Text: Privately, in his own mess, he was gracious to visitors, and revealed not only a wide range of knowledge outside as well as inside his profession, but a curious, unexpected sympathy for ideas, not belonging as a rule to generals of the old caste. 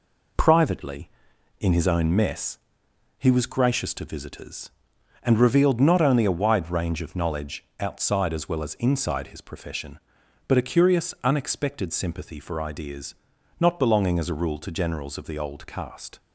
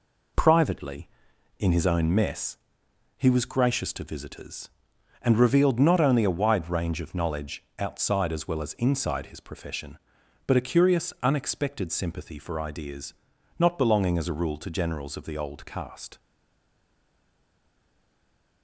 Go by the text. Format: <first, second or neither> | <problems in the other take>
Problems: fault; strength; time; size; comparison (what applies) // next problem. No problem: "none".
first | pauses between "knowledge" and "outside"; slight; at 7.6 s; 0.16 s long; slight in the first // stays silent after the last word; from 16.1 s on; 2.5 s long